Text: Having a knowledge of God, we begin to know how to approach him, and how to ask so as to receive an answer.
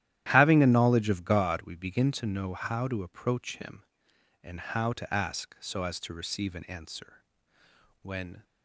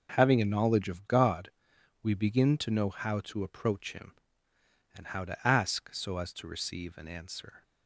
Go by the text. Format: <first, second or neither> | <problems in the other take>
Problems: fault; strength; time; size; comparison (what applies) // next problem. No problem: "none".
second | starts louder than the rest; strong; until 1.3 s; 12.5 dB // goes on to say "When"; slight; from 8.0 s on; 0.40 s long